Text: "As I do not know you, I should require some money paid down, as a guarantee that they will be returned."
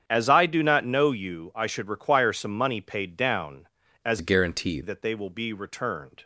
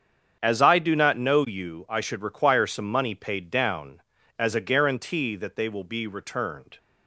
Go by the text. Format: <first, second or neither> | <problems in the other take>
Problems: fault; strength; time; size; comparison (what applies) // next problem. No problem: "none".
second | starts louder than the rest; strong; until 1.0 s; 8 dB; strong in the second // changes voice from "a" to "guarantee"; from 4.1 to 4.8 s; 0.7 s long